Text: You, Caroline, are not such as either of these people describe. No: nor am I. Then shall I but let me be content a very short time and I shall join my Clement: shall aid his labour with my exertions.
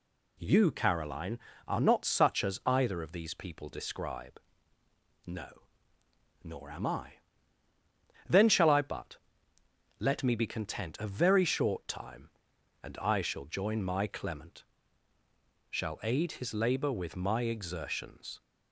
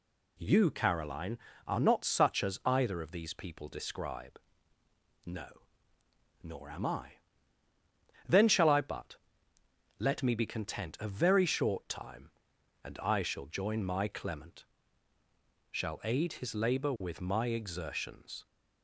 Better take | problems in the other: neither | pauses between "but" and "let"; noticeable; the same in both

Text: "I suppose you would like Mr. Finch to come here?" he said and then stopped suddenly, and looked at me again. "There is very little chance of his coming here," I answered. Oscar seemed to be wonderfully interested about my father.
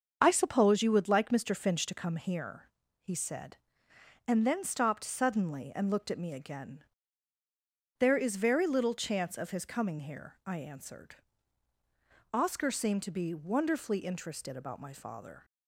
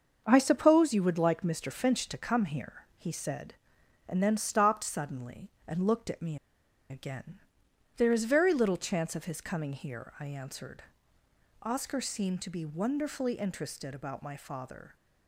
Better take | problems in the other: first | starts louder than the rest; until 1.2 s; 6.5 dB; also in the first // pauses between "me" and "again"; noticeable; at 6.3 s; 0.52 s long

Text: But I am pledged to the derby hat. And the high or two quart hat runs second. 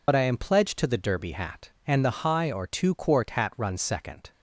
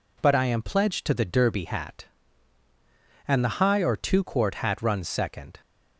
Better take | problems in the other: second | loses the start of "But"; at 0.0 s; 45 ms

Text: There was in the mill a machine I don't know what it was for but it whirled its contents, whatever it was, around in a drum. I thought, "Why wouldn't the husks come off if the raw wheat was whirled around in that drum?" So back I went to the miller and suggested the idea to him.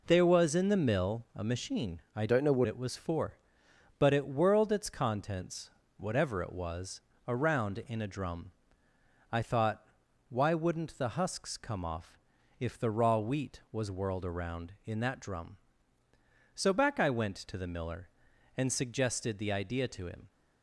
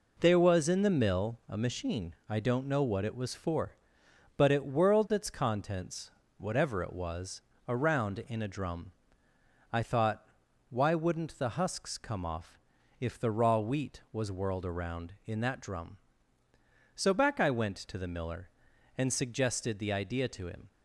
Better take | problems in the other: second | changes voice from "don't" to "what"; from 2.2 to 2.6 s; 0.4 s long // pauses between "off" and "if"; at 12.1 s; 0.42 s long; also in the second

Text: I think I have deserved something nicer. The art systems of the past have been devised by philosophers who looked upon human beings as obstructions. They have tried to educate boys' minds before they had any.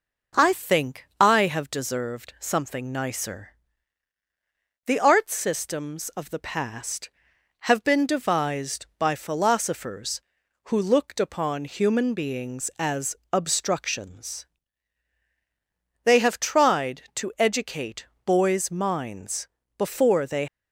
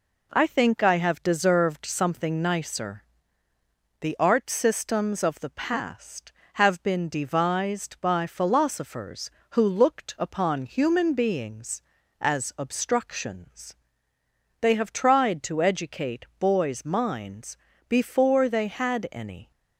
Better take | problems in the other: second | pauses between "think" and "I"; slight; at 1.0 s; 0.16 s long // pauses between "as" and "obstructions"; slight; at 13.1 s; 0.18 s long // pauses between "educate" and "boys"; slight; at 18.0 s; 0.20 s long // pauses between "minds" and "before"; slight; at 19.4 s; 0.32 s long; slight in the second // stops before "had any"; at 20.4 s

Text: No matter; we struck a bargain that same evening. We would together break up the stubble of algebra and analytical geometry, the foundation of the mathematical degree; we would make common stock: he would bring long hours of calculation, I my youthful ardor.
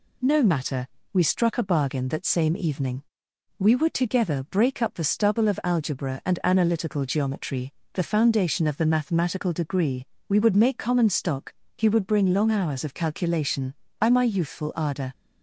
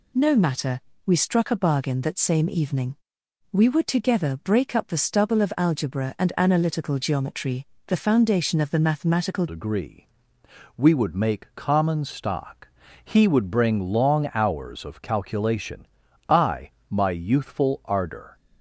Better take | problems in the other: first | changes voice at "degree"; from 9.4 s on; 8.9 s long // pauses between "I" and "my"; slight; at 16.7 s; 0.18 s long

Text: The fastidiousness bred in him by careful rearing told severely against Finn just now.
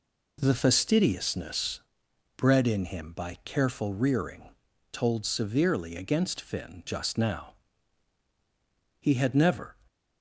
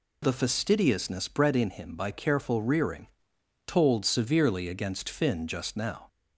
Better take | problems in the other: second | pauses between "fastidiousness" and "bred"; noticeable; at 1.8 s; 0.56 s long // pauses between "rearing" and "told"; noticeable; at 4.4 s; 0.50 s long; noticeable in the second // goes on to say "He had never"; noticeable; from 9.0 s on; 0.74 s long

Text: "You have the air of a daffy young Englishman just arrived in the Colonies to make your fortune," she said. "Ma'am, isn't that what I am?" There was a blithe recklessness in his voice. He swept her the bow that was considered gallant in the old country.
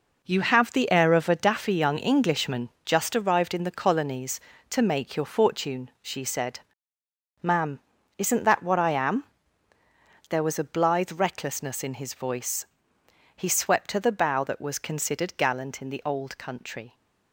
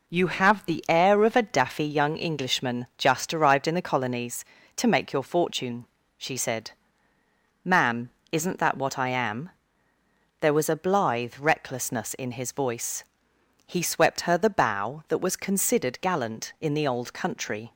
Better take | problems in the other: second | gets quieter; strong; throughout; 8.5 dB

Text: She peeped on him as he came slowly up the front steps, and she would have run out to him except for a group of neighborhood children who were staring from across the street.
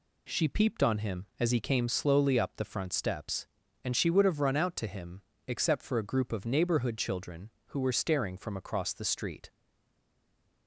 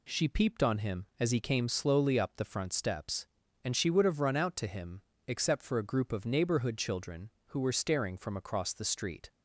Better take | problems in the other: second | pauses between "him" and "except"; slight; at 5.2 s; 0.26 s long; slight in the second // stays silent after the last word; noticeable; from 9.5 s on; 1.1 s long

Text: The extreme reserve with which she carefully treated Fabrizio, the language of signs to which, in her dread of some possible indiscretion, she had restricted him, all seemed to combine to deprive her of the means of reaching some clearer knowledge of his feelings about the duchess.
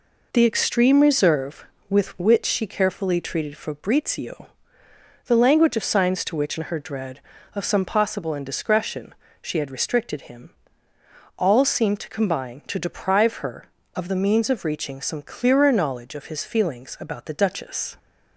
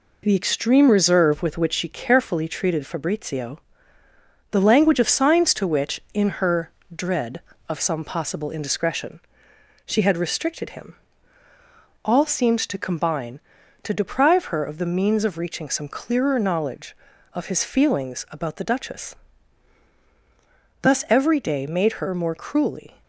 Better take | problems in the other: first | pauses between "her" and "dread"; slight; at 6.7 s; 0.24 s long // goes on to say "Thus every day made her more cruelly"; strong; from 20.8 s on; 2.2 s long

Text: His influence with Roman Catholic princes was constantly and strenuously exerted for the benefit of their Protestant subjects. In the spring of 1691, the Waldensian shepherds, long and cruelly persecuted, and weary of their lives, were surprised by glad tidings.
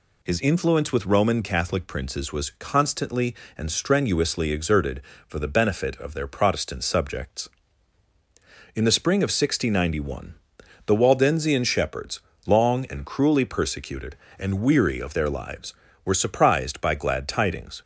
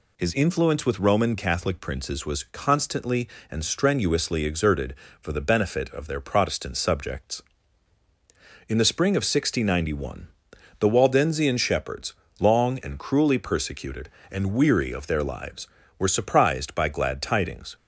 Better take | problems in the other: neither | none

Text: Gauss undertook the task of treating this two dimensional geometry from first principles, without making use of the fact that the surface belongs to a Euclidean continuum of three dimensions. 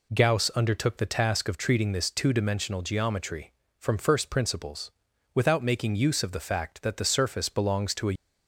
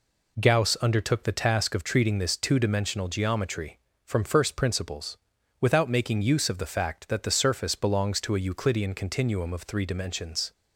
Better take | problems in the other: second | stops before "Euclidean continuum of three dimensions"; at 8.1 s

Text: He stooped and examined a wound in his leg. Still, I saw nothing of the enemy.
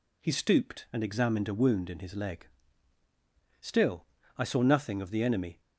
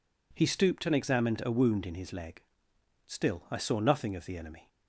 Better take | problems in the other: neither | none

